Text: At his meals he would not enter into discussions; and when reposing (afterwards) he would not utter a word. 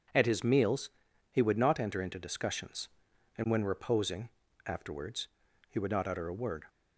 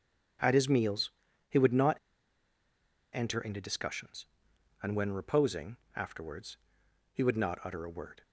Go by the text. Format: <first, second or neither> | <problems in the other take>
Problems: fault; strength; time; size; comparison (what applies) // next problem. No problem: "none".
first | pauses between "meals" and "he"; at 1.0 s; 0.40 s long; also in the first // pauses between "not" and "enter"; at 1.9 s; 1.1 s long